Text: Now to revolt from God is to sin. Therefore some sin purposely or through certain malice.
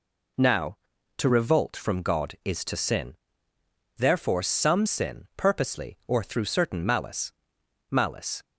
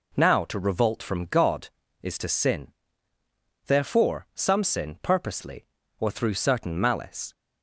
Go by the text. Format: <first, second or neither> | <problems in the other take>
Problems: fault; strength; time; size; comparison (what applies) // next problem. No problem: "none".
second | says "malice" twice; at 7.9 s